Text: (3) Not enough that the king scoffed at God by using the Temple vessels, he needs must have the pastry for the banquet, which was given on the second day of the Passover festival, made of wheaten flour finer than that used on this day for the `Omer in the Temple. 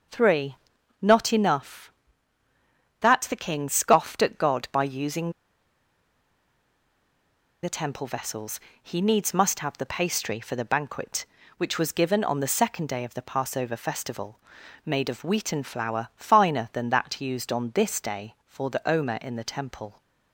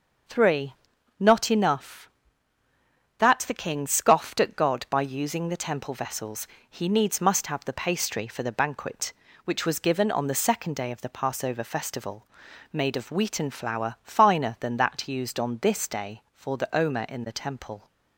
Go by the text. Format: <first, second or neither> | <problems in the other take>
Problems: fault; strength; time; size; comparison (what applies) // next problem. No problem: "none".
second | starts louder than the rest; until 1.5 s; 6.5 dB; also in the second // pauses between "using" and "the"; strong; at 5.3 s; 2.3 s long